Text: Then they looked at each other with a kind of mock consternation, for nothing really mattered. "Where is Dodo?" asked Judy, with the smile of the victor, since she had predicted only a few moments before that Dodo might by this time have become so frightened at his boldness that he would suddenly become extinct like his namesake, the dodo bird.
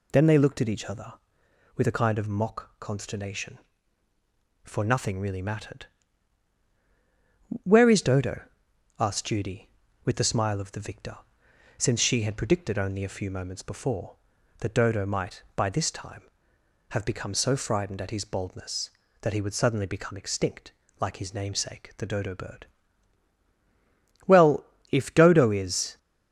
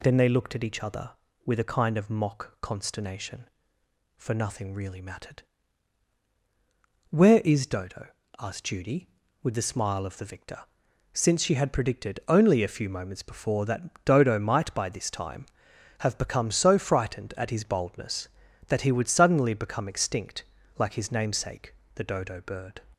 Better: second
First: pauses between "extinct" and "like"; slight; at 20.7 s; 0.28 s long // goes on to say "Well if Dodo is"; strong; from 24.2 s on; 1.7 s long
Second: pauses between "extinct" and "like"; slight; at 20.4 s; 0.36 s long

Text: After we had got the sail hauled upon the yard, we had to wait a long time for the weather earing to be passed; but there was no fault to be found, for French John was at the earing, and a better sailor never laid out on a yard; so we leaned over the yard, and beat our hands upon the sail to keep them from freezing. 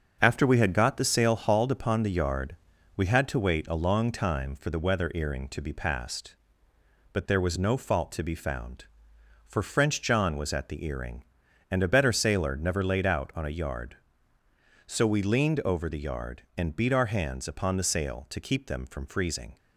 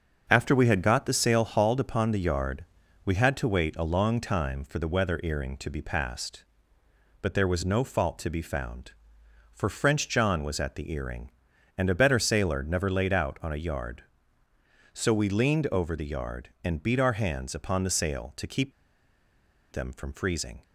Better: first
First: starts louder than the rest; until 1.2 s; 7 dB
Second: starts louder than the rest; until 1.2 s; 7 dB // pauses between "keep" and "them"; at 18.7 s; 1.0 s long

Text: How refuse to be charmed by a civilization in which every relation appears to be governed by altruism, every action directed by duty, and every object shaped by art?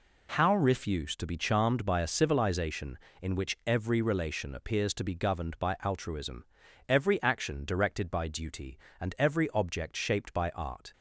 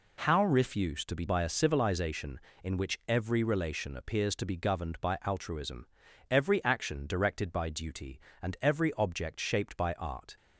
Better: first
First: none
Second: skips "charmed"; at 1.2 s

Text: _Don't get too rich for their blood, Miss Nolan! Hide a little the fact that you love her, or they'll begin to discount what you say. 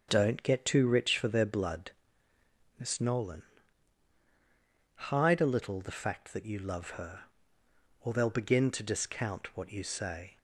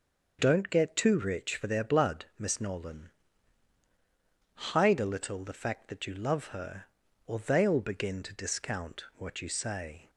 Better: neither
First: starts louder than the rest; until 1.1 s; 7 dB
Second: starts louder than the rest; noticeable; until 1.4 s; 6 dB

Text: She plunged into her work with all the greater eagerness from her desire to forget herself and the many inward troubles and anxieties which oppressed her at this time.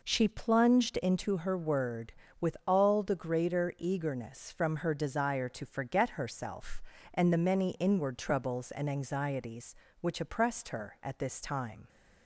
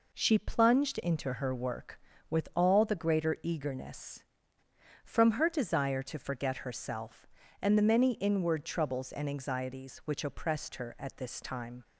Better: second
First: says "word" for "work"; at 1.5 s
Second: none

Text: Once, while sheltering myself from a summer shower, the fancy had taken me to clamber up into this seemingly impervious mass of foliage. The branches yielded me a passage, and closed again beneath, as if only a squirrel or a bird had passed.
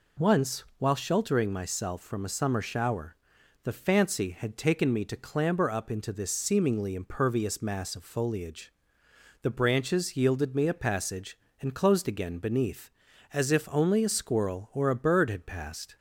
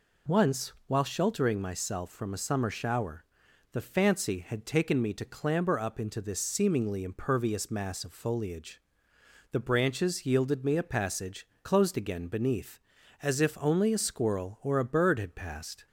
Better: first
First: none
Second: skips "and"; at 11.5 s

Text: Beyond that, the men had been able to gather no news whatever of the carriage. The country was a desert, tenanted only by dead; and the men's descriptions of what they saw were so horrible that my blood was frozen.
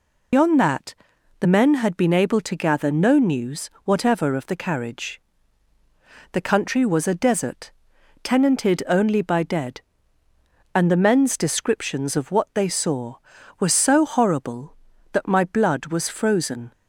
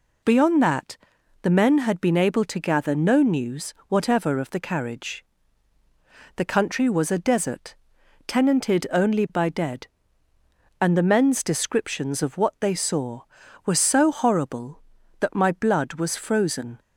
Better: second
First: loses the start of "Beyond"; at 0.3 s; 110 ms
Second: none

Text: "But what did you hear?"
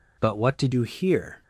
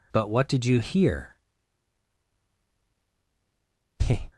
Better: second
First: changes voice at "you"; from 0.7 s on; 0.7 s long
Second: none

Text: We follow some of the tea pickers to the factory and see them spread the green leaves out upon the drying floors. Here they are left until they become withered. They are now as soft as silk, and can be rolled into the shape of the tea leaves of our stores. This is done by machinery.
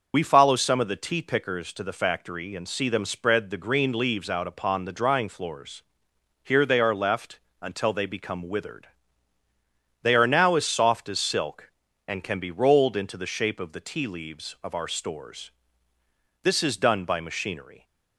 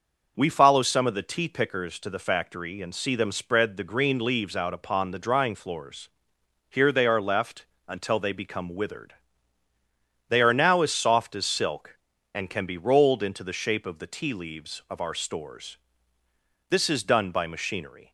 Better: second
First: loses the start of "We"; at 0.1 s; 35 ms // pauses between "left" and "until"; slight; at 7.3 s; 0.24 s long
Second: pauses between "left" and "until"; slight; at 7.6 s; 0.24 s long

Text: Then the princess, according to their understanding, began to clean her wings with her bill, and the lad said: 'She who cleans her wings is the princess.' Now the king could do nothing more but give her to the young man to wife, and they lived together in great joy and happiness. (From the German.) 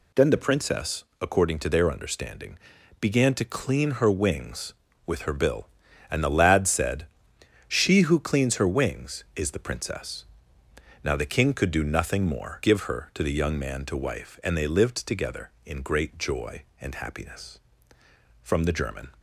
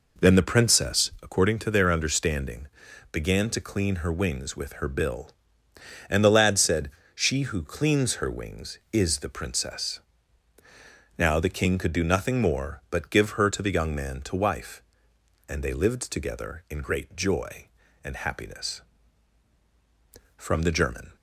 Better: second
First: skips "but"; at 12.6 s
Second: none

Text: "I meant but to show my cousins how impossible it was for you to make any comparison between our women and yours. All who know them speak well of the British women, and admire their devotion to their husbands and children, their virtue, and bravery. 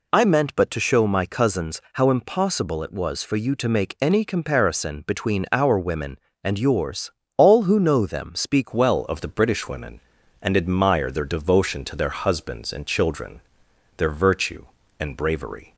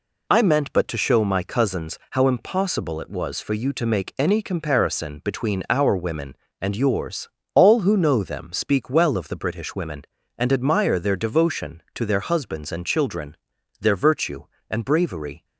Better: second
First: changes voice at "well"; from 8.7 s on; 7.0 s long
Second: none

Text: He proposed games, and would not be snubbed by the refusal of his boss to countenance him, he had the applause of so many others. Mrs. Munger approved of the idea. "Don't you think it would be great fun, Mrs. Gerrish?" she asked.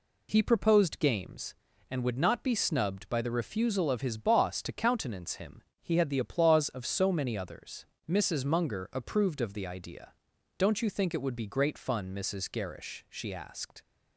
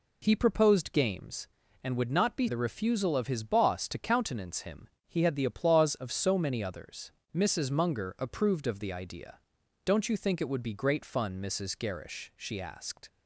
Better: first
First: none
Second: skips "snubbed by"; at 2.4 s

